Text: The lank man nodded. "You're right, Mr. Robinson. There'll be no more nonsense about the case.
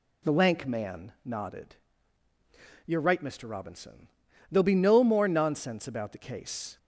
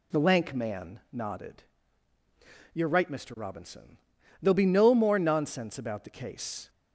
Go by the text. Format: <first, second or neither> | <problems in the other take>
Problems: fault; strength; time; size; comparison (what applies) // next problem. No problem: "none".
neither | none